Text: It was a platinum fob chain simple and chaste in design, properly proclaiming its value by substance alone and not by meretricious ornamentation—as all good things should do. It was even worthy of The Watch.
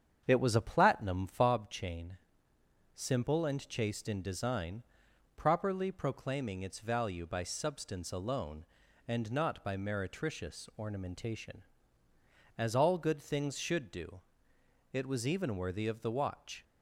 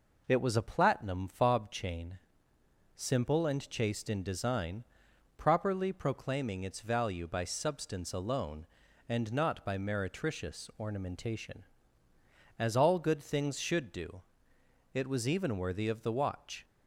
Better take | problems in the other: second | starts louder than the rest; strong; until 1.5 s; 8 dB // pauses between "chain" and "simple"; noticeable; at 2.1 s; 0.78 s long; noticeable in the second

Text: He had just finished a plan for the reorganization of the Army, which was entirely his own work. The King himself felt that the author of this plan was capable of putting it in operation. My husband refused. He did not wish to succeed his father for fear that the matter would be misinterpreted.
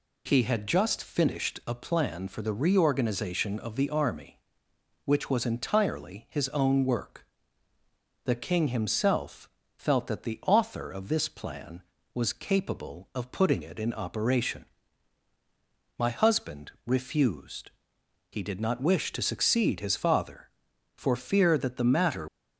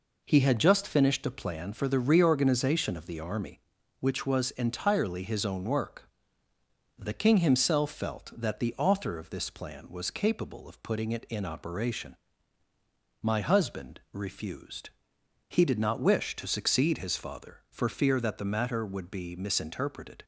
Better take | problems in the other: second | pauses between "himself" and "felt"; slight; at 9.4 s; 0.28 s long // stops before "would be misinterpreted"; at 22.2 s

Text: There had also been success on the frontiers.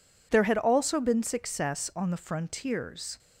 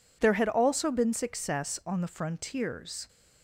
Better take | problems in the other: neither | none

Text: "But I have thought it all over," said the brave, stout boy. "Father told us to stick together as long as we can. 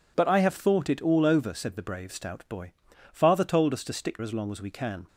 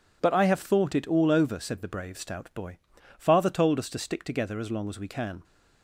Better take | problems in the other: second | skips "together"; at 4.1 s

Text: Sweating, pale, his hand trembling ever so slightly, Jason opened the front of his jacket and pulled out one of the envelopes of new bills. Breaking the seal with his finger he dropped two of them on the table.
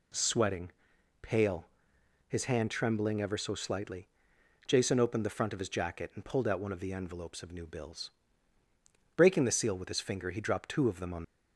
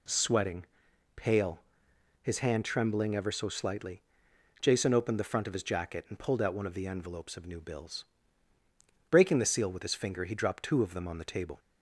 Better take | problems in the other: second | stops before "the table"; at 11.2 s

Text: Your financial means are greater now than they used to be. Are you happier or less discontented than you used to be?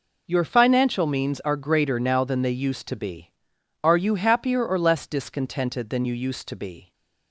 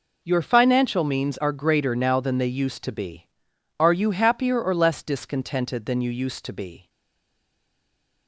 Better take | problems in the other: first | stays silent after the last word; noticeable; from 6.8 s on; 1.4 s long

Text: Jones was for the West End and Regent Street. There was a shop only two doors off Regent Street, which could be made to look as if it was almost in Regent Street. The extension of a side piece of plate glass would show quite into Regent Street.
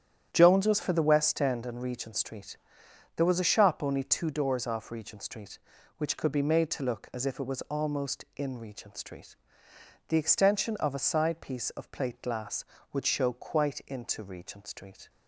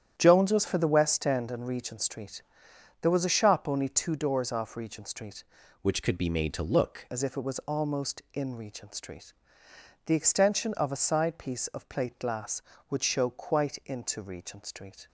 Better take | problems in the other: first | starts louder than the rest; strong; until 1.1 s; 10 dB; strong in the first // changes voice from "which" to "look"; from 5.8 to 7.0 s; 1.2 s long

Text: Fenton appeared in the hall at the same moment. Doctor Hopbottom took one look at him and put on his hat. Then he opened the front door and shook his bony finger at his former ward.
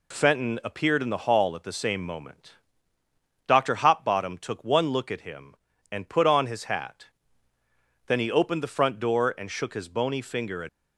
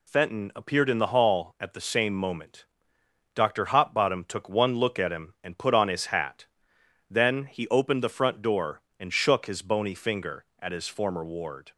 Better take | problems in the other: second | stops before "his former ward"; at 10.6 s

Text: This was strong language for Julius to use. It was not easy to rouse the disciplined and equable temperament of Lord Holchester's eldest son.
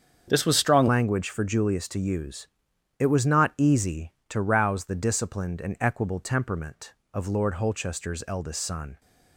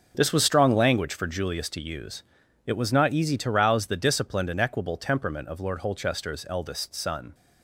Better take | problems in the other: second | starts louder than the rest; strong; until 1.2 s; 7.5 dB; also in the second // changes voice at "language"; from 0.8 s on; 8.1 s long

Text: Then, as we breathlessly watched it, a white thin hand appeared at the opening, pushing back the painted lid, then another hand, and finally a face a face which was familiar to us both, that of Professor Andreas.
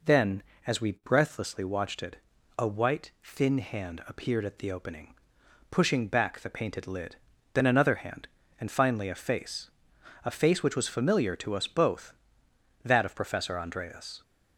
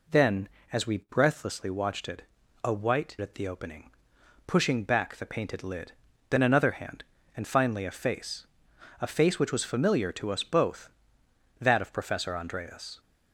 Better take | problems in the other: first | skips "thin hand appeared"; at 3.1 s // pauses between "face" and "a"; noticeable; at 8.4 s; 0.56 s long; noticeable in the first

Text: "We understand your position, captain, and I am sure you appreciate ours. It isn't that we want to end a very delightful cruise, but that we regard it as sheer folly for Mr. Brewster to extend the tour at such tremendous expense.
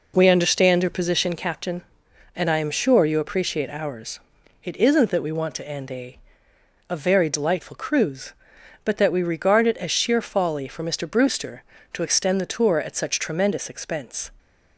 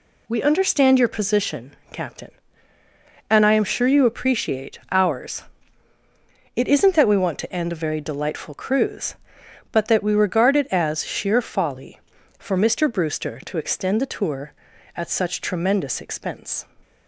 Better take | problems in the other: second | says "a" twice; at 6.8 s

